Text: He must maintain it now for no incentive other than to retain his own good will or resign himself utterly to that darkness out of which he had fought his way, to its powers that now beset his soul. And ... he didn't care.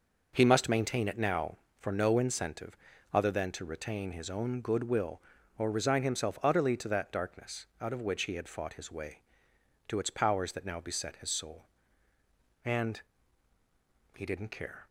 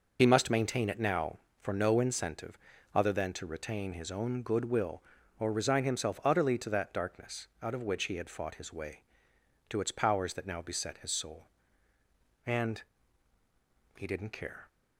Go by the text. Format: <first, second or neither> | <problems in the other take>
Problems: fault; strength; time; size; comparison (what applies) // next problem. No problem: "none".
first | loses the start of "He"; at 0.1 s; 40 ms // pauses between "incentive" and "other"; at 2.5 s; 0.38 s long; also in the first